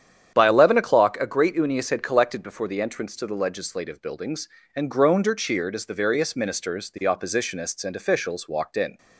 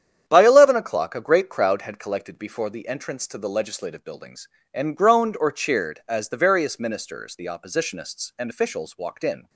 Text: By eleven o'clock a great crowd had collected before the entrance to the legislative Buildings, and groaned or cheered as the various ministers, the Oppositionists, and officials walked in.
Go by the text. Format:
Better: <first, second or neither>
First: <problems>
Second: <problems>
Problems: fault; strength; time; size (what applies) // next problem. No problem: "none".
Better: second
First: starts louder than the rest; strong; until 1.3 s; 9 dB // says "unius" for "crowd"; at 1.5 s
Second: starts louder than the rest; strong; until 1.2 s; 9 dB